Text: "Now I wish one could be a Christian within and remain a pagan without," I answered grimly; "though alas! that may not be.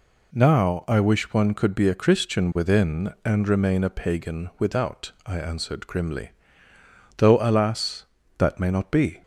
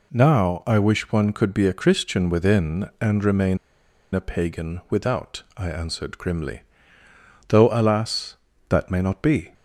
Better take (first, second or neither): first